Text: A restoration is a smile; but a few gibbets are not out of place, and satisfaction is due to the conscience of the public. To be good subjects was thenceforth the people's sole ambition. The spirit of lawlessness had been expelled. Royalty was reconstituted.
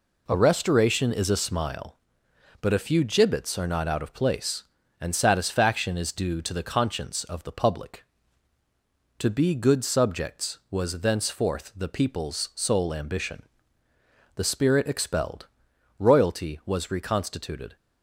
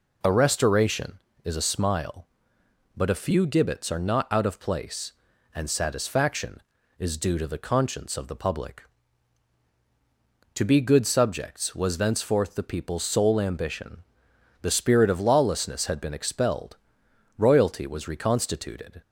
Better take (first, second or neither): second